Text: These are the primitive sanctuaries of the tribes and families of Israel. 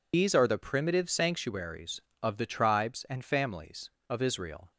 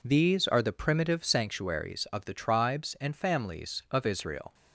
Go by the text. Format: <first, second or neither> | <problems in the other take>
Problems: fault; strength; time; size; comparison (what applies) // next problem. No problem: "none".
second | loses the start of "These"; at 0.1 s; 110 ms